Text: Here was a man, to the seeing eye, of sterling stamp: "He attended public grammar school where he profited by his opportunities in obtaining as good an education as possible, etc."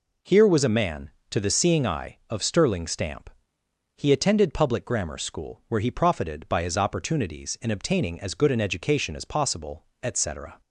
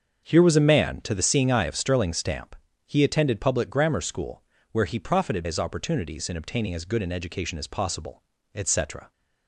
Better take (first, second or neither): first